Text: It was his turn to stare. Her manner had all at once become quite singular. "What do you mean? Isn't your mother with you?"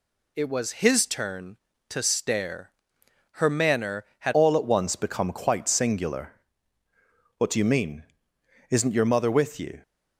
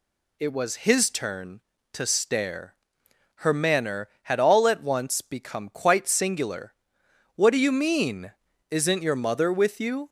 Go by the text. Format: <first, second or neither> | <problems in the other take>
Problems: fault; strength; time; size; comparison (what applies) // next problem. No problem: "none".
second | changes voice at "all"; from 4.3 s on; 5.5 s long